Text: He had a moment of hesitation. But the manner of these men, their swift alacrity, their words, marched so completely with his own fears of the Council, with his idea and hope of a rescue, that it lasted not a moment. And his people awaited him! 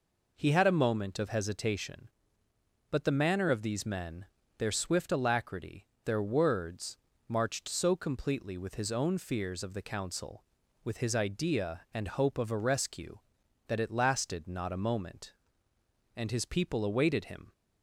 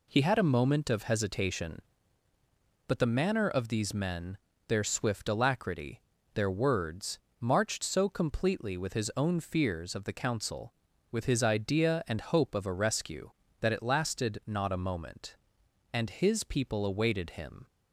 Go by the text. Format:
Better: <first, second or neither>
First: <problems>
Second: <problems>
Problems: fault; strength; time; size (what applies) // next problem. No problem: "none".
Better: neither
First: none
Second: none